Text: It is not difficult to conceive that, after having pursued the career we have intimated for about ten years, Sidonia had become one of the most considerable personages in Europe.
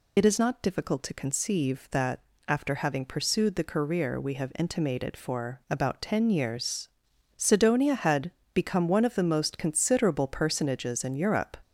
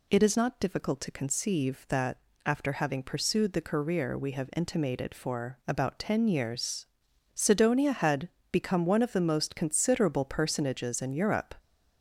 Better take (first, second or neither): second